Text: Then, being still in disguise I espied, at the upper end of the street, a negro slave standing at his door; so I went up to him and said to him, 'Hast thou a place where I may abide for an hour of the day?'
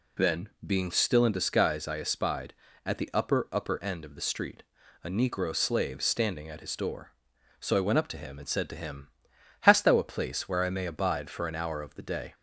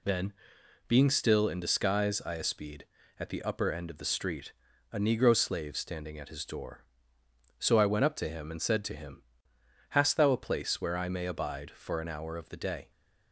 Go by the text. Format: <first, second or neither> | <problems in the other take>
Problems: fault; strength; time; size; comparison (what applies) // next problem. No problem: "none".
second | says "upper" twice; at 3.5 s